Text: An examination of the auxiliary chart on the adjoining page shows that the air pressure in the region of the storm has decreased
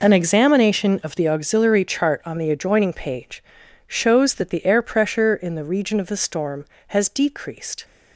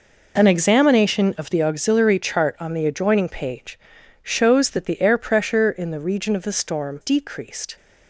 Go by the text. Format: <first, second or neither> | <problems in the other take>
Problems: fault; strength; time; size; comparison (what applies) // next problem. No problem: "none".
first | pauses between "page" and "shows"; at 3.7 s; 0.44 s long; also in the first // skips "has"; at 7.0 s